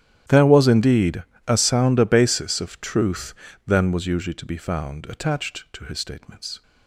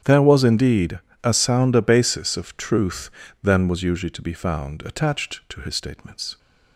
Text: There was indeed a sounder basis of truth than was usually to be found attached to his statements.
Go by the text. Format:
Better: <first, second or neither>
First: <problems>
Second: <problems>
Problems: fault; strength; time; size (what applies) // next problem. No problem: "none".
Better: second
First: gets quieter; strong; throughout; 21.5 dB // starts louder than the rest; strong; until 1.5 s; 11.5 dB // pauses between "indeed" and "a"; slight; at 1.2 s; 0.24 s long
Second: starts louder than the rest; strong; until 1.2 s; 9.5 dB // pauses between "indeed" and "a"; slight; at 1.0 s; 0.24 s long